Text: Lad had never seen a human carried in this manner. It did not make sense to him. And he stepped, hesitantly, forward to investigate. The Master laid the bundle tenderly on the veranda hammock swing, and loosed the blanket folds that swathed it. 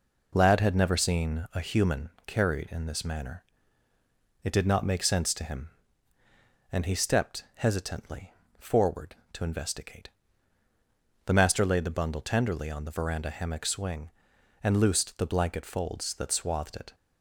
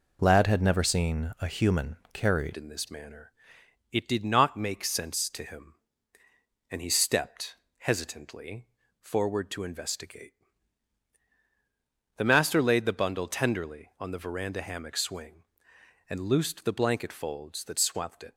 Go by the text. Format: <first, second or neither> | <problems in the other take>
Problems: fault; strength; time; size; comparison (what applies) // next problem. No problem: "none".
first | pauses between "human" and "carried"; slight; at 1.9 s; 0.16 s long; slight in the first // changes voice at "in"; from 2.5 s on; 15.8 s long